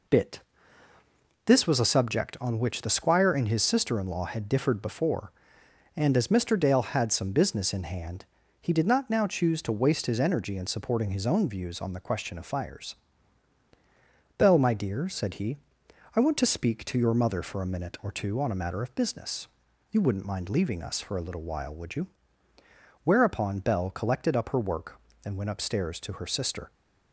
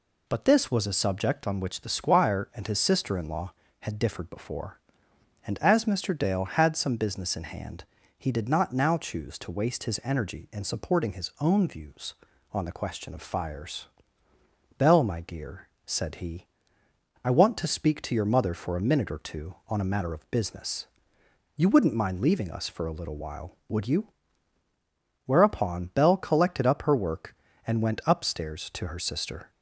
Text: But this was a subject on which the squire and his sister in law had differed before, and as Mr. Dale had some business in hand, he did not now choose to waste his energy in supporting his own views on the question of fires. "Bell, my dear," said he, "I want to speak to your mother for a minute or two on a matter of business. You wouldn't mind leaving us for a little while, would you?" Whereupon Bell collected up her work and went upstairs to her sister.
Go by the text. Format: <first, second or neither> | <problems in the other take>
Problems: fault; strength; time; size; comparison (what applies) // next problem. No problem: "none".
second | says "Bit" for "But"; at 0.0 s